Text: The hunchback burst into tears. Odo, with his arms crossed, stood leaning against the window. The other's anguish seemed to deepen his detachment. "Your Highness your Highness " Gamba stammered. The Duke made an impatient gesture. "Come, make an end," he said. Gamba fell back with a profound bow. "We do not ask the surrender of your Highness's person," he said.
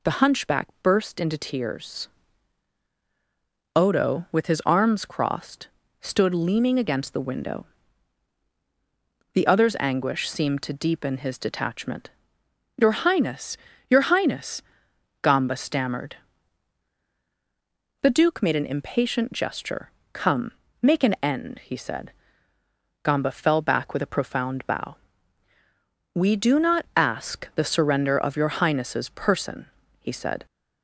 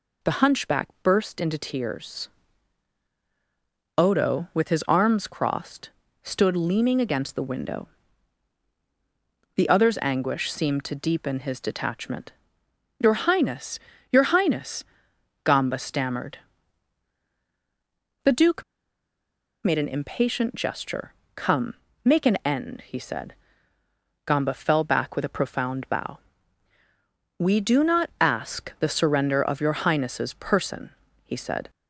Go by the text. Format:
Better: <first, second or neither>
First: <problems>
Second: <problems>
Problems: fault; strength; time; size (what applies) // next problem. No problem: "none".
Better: first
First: pauses between "Highness" and "your"; slight; at 13.5 s; 0.32 s long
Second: pauses between "Highness" and "your"; slight; at 13.7 s; 0.32 s long // pauses between "Duke" and "made"; at 18.6 s; 1.0 s long